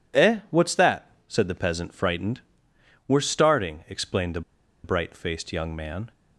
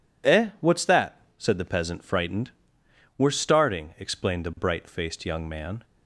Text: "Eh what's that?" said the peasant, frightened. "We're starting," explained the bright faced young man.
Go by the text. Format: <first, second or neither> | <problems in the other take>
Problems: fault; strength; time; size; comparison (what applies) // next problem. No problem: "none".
second | pauses between "the" and "bright"; at 4.4 s; 0.43 s long